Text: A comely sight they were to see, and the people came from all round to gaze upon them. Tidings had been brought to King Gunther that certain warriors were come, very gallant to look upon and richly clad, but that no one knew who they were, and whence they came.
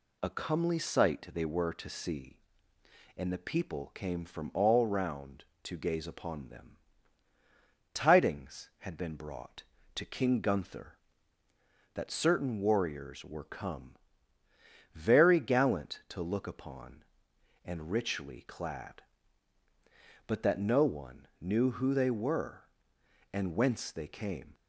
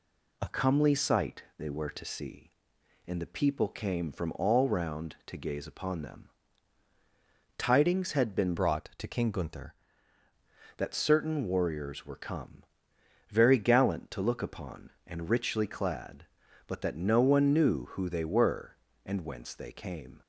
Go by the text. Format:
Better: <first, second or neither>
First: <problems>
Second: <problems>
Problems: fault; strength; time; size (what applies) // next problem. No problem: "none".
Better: first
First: none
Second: pauses between "sight" and "they"; slight; at 1.4 s; 0.16 s long // changes voice from "brought" to "Gunther"; from 8.5 to 9.7 s; 1.2 s long